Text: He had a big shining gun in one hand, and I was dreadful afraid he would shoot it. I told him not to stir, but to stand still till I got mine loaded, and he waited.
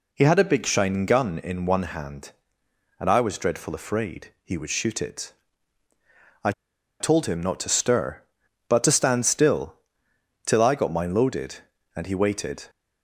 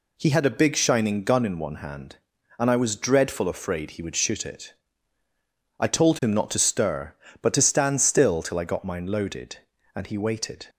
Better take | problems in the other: second | pauses between "I" and "told"; noticeable; at 6.5 s; 0.48 s long // pauses between "still" and "till"; noticeable; at 9.7 s; 0.70 s long

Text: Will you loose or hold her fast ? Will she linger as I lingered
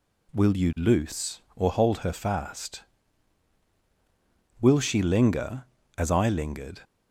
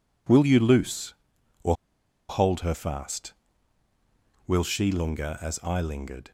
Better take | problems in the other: first | pauses between "or" and "hold"; noticeable; at 1.7 s; 0.55 s long

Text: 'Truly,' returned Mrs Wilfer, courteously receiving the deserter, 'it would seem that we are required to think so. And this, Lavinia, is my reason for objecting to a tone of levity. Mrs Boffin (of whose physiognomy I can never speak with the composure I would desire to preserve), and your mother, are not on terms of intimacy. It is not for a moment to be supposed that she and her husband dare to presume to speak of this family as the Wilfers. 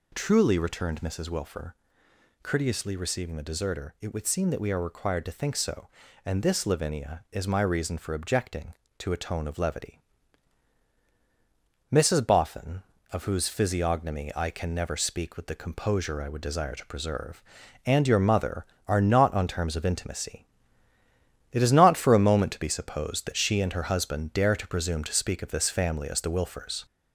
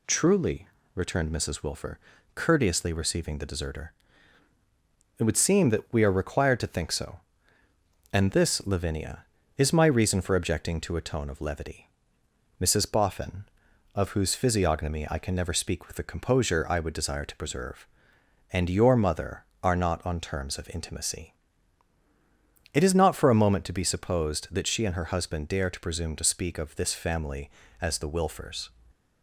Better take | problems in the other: second | gets louder; noticeable; throughout; 4 dB

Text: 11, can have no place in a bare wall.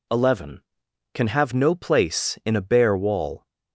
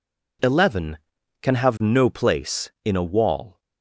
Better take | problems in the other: first | skips "bare"; at 3.0 s

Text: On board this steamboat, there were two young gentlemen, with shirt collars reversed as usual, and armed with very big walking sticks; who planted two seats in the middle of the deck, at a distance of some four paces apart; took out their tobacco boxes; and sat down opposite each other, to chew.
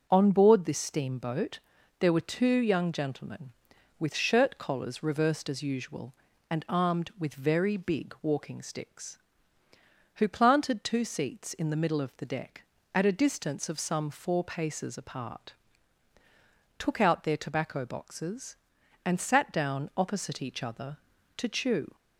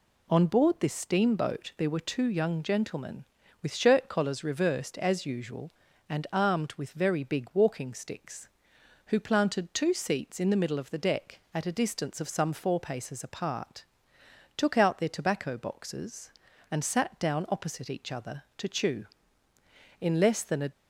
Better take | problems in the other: first | goes on to say "In less than a"; noticeable; from 19.9 s on; 0.72 s long

